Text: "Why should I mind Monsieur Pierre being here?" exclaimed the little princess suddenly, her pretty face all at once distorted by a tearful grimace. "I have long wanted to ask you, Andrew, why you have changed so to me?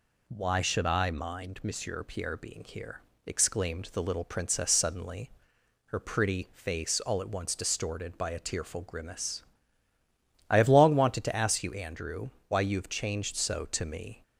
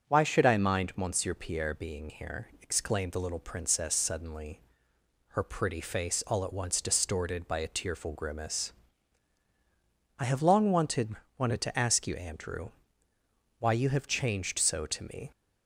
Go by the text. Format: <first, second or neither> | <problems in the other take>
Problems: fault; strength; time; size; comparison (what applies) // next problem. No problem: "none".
first | starts louder than the rest; strong; until 1.1 s; 7 dB // says "wanted" twice; at 11.3 s